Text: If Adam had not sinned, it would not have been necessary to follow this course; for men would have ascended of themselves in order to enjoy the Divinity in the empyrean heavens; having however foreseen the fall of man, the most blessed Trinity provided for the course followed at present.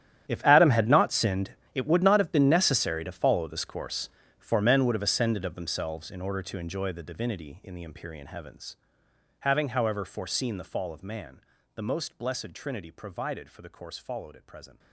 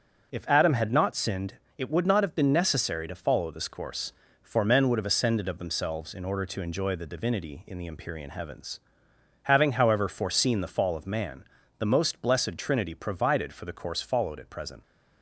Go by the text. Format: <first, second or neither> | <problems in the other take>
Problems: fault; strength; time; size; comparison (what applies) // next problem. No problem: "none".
second | gets quieter; strong; throughout; 18 dB